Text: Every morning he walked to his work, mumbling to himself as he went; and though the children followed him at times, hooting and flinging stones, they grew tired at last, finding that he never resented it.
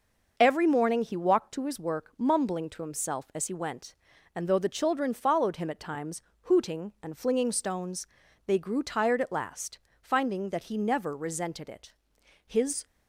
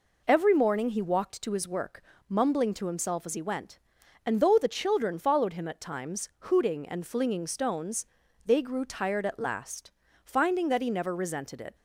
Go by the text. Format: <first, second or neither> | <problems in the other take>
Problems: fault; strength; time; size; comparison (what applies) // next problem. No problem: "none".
second | starts louder than the rest; noticeable; until 1.3 s; 6 dB // goes on to say "His"; slight; from 12.4 s on; 0.38 s long